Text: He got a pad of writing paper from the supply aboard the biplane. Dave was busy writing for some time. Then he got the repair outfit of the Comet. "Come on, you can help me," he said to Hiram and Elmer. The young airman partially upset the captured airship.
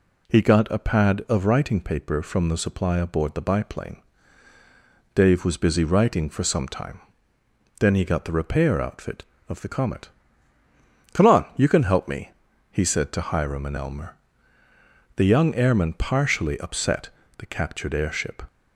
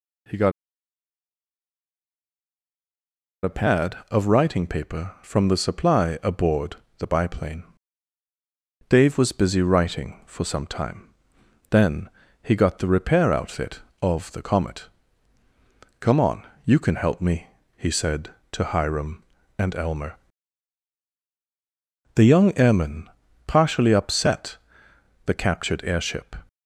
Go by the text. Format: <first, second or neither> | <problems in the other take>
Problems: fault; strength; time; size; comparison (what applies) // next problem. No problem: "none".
first | pauses between "got" and "a"; strong; at 0.5 s; 2.9 s long // pauses between "aboard" and "the"; slight; at 6.7 s; 0.22 s long // pauses between "Then" and "he"; slight; at 12.0 s; 0.32 s long // pauses between "airman" and "partially"; at 23.0 s; 0.38 s long // pauses between "upset" and "the"; noticeable; at 24.5 s; 0.68 s long; slight in the first